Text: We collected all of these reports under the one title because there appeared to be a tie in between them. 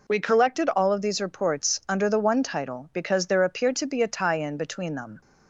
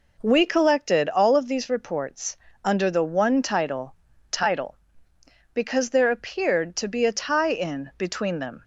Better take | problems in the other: first | pauses between "reports" and "under"; slight; at 2.3 s; 0.28 s long // says "title" twice; at 4.3 s

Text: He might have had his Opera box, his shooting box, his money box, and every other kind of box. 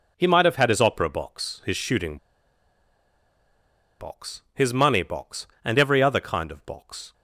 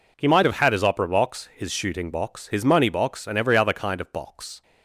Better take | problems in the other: second | pauses between "shooting" and "box"; strong; at 2.1 s; 1.8 s long

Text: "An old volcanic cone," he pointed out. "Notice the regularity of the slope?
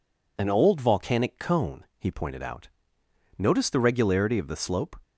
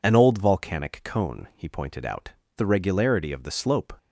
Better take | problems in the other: first | skips "Notice"; at 2.4 s

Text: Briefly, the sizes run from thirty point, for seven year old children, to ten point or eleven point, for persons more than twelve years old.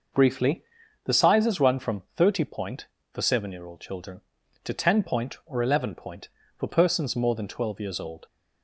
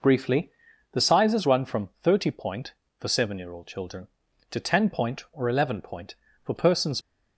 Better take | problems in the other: first | stops before "more than twelve years old"; at 7.0 s

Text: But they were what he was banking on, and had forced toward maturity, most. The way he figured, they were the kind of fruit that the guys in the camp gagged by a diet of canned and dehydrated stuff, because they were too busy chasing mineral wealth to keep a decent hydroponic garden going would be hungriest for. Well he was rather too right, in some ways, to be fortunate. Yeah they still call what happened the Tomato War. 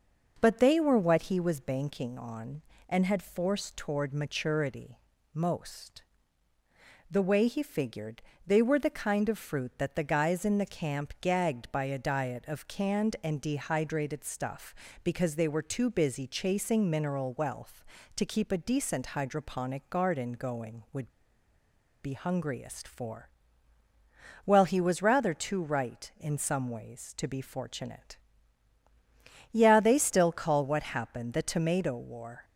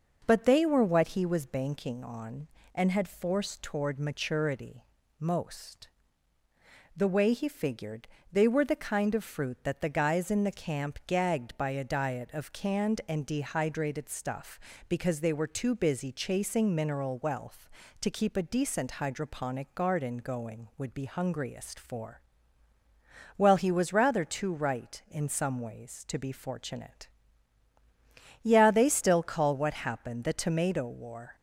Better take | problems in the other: second | pauses between "would" and "be"; noticeable; at 21.0 s; 0.94 s long

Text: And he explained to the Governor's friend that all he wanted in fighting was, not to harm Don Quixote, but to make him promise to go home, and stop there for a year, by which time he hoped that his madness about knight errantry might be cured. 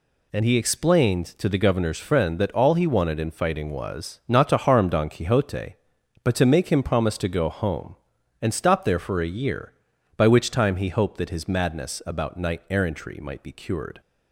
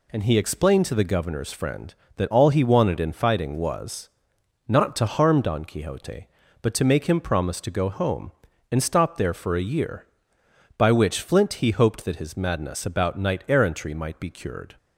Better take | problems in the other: first | says "flint" for "time"; at 11.2 s

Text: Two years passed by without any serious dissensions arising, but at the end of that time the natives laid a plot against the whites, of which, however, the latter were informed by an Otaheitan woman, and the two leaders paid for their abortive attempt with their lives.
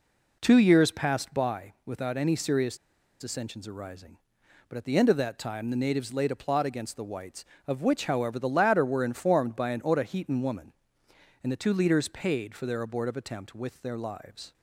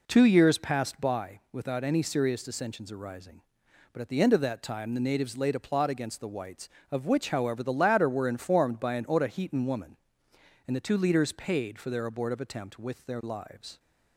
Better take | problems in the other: second | pauses between "serious" and "dissensions"; at 2.7 s; 0.43 s long

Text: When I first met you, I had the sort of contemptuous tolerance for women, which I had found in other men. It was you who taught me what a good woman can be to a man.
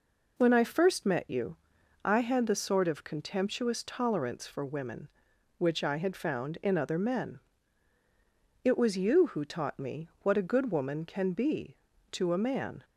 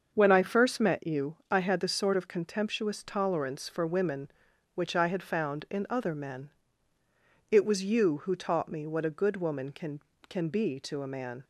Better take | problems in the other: first | starts louder than the rest; until 1.1 s; 6.5 dB // says "can" twice; at 10.2 s

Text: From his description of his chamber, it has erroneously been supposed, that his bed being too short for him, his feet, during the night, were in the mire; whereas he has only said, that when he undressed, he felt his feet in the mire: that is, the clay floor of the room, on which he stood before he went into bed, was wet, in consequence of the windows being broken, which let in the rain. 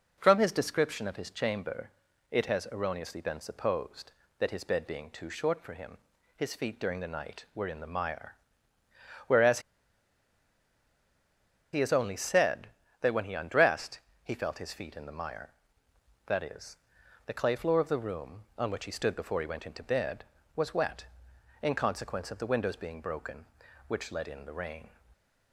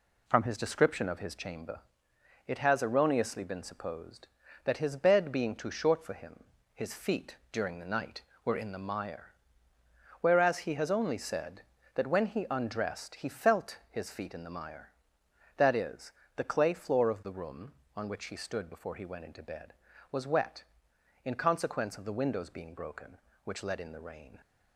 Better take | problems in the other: second | pauses between "whereas" and "he"; strong; at 9.6 s; 2.1 s long

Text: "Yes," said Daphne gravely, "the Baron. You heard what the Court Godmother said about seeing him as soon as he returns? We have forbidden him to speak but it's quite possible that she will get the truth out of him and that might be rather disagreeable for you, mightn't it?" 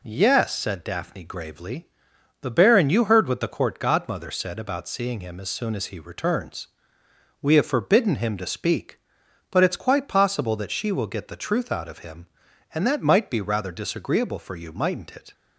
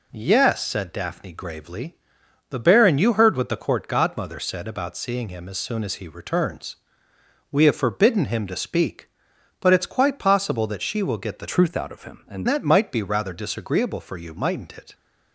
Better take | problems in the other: first | changes voice from "truth" to "and"; from 11.5 to 12.4 s; 0.9 s long

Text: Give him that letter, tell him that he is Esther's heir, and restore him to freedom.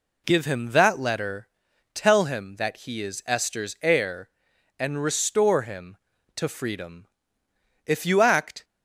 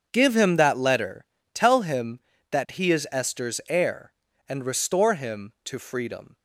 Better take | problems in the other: second | goes on to say "If you act"; noticeable; from 7.8 s on; 0.78 s long

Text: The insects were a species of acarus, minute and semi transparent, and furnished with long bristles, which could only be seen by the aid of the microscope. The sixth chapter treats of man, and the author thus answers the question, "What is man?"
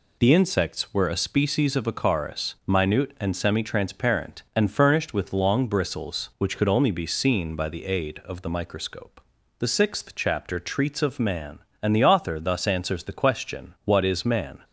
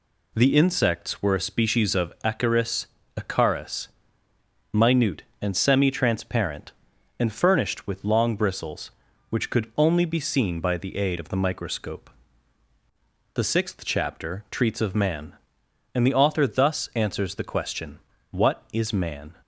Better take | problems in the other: first | says "acarus" twice; at 3.1 s

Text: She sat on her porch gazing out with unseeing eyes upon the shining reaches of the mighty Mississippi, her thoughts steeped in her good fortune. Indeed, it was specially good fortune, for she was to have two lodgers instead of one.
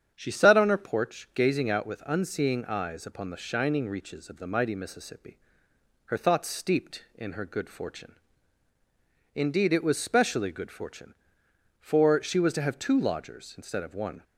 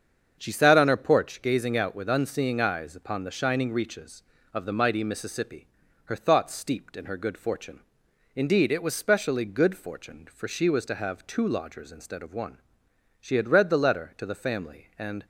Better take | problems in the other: first | starts louder than the rest; strong; until 1.3 s; 7.5 dB; strong in the first // goes on to say "She had read the letter to the family and"; strong; from 13.1 s on; 2.0 s long

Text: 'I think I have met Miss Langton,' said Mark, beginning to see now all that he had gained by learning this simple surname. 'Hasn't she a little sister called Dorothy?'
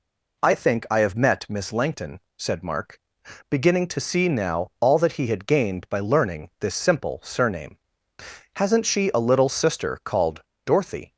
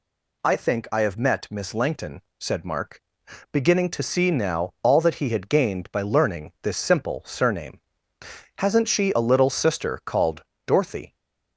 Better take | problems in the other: second | starts louder than the rest; slight; until 1.8 s; 2.5 dB // pauses between "called" and "Dorothy"; slight; at 10.4 s; 0.24 s long; slight in the second

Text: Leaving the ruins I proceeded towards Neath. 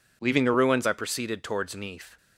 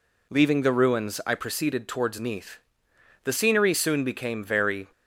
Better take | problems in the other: first | goes on to say "The scenery soon became very"; strong; from 3.2 s on; 1.6 s long

